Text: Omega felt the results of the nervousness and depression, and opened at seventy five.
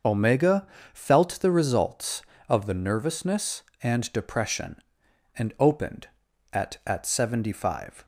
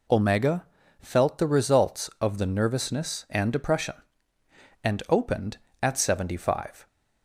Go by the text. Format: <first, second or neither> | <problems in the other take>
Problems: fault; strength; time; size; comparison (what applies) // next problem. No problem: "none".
second | starts louder than the rest; noticeable; until 1.3 s; 6 dB // pauses between "Omega" and "felt"; slight; at 0.6 s; 0.28 s long; slight in the second // says "at" twice; at 6.8 s